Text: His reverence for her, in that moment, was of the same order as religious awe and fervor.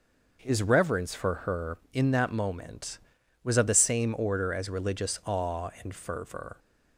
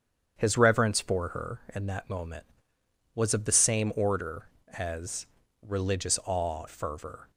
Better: first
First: none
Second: starts louder than the rest; strong; until 1.3 s; 8 dB // pauses between "as" and "religious"; slight; at 5.2 s; 0.36 s long // skips "and"; at 6.6 s

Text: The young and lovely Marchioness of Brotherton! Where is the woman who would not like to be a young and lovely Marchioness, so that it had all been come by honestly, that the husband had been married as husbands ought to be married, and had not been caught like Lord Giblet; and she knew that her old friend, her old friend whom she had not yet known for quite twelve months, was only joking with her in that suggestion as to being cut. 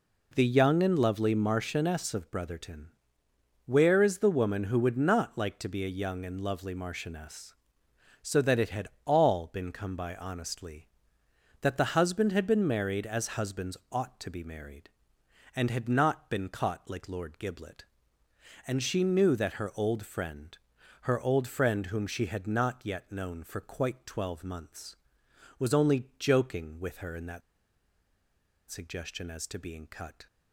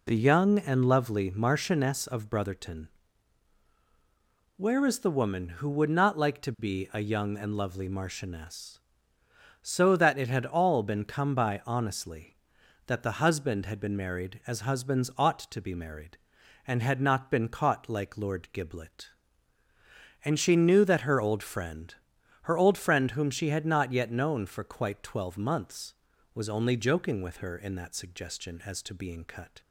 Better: second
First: pauses between "had" and "all"; slight; at 8.8 s; 0.16 s long // pauses between "that" and "suggestion"; strong; at 27.4 s; 1.2 s long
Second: none

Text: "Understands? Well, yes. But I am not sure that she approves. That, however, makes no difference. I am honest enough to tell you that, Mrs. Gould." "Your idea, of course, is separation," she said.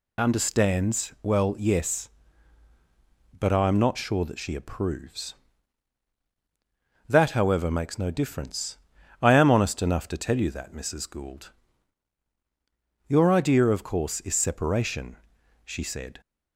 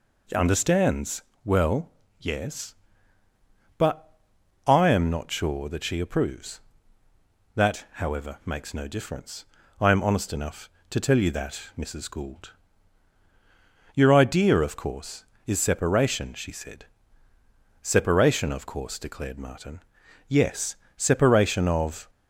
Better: first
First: none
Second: pauses between "But" and "I"; noticeable; at 4.1 s; 0.50 s long // goes on to say "Separation of course declared Martin Yes separation of"; strong; from 17.8 s on; 4.2 s long

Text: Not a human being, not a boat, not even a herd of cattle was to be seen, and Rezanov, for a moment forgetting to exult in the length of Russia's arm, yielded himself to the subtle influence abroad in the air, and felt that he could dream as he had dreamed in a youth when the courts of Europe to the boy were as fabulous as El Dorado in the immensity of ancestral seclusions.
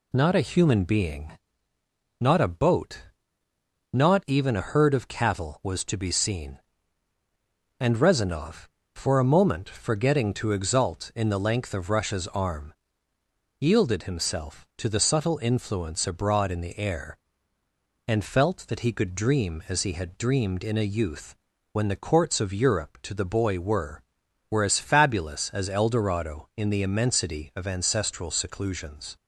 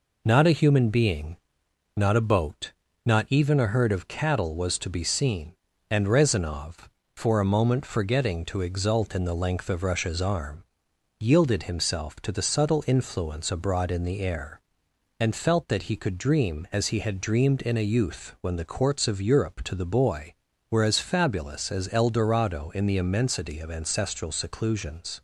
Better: second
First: pauses between "youth" and "when"; slight; at 21.3 s; 0.36 s long // says "were" twice; at 24.4 s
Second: none

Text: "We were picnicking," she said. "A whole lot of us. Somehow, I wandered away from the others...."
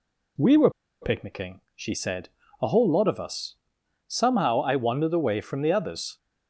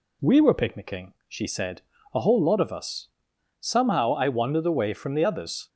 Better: second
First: pauses between "were" and "picnicking"; slight; at 0.6 s; 0.31 s long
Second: none

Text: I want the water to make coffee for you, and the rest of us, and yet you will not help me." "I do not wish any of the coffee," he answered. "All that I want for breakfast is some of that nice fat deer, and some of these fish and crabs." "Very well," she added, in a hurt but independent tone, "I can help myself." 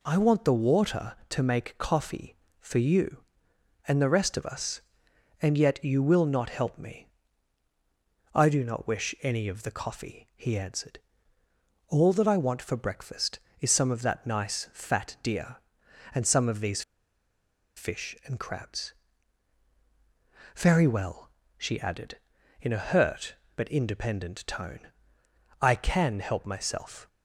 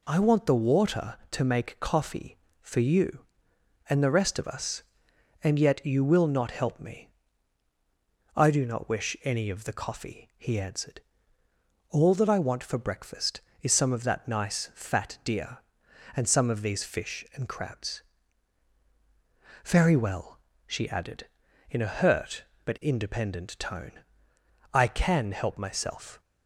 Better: second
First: pauses between "these" and "fish"; noticeable; at 16.8 s; 0.95 s long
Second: none

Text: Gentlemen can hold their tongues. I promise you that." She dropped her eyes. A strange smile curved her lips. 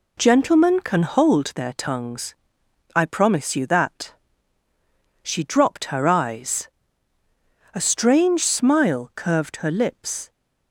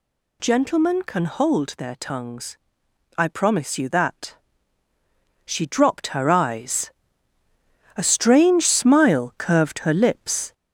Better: first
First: none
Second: gets louder; throughout; 3.5 dB

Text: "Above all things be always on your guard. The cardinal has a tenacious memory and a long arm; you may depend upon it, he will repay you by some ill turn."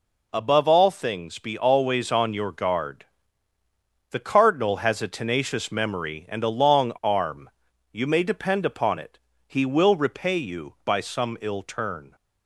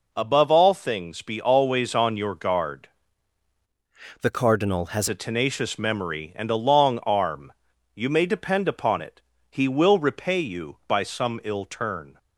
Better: first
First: none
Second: changes voice from "The" to "has"; from 4.2 to 5.0 s; 0.8 s long

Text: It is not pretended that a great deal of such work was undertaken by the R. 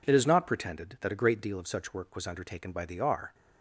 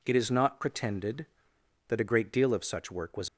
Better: first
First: none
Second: stops before "undertaken by the R"; at 3.2 s

